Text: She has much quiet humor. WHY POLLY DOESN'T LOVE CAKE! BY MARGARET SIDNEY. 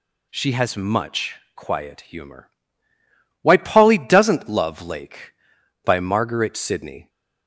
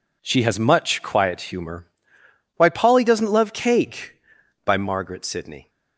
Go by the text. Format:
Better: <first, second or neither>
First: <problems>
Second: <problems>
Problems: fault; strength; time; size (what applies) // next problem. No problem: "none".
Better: second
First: pauses between "much" and "quiet"; slight; at 1.3 s; 0.18 s long // says "Lake" for "CAKE"; at 4.8 s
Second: none